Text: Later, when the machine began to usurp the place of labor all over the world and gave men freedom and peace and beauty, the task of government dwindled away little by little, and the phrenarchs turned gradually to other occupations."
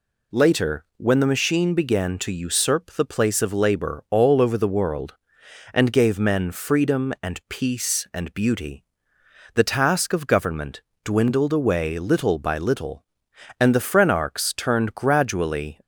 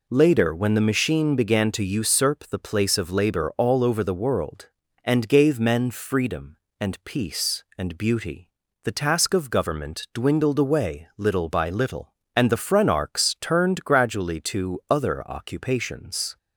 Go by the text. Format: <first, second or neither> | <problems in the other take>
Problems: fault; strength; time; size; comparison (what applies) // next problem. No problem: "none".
second | pauses between "government" and "dwindled"; slight; at 10.8 s; 0.24 s long // stops before "to other occupations"; at 15.8 s